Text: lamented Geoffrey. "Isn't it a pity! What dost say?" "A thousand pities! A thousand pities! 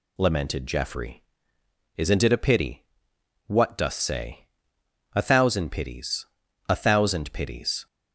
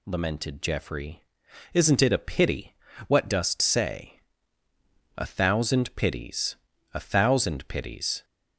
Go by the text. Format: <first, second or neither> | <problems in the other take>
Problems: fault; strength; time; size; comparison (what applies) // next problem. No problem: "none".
neither | none